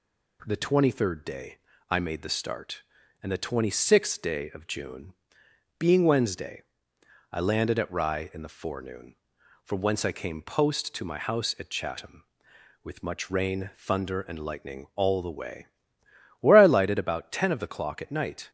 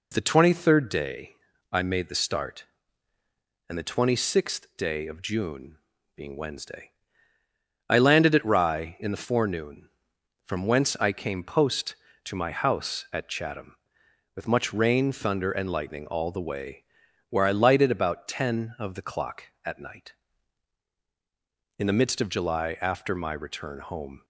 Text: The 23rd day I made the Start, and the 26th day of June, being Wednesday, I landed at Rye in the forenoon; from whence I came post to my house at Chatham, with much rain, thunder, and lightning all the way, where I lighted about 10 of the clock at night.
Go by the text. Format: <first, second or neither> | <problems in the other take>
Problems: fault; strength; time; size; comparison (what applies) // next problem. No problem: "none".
first | pauses between "day" and "I"; slight; at 1.3 s; 0.34 s long; slight in the first // goes on to say "In the midst of July after my return home"; strong; from 21.7 s on; 2.4 s long